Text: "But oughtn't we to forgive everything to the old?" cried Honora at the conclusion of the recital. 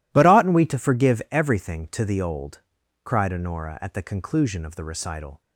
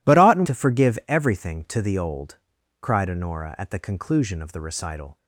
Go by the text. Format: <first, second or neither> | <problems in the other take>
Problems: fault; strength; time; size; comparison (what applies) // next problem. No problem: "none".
first | skips "we"; at 0.4 s